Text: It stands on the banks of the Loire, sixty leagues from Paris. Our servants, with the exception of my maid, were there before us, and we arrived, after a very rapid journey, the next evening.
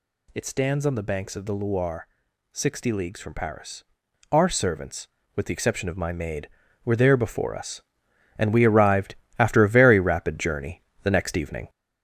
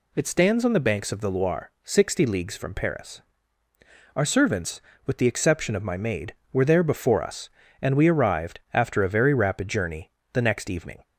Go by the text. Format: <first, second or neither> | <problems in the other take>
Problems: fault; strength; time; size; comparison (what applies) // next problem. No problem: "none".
second | gets louder; noticeable; throughout; 4 dB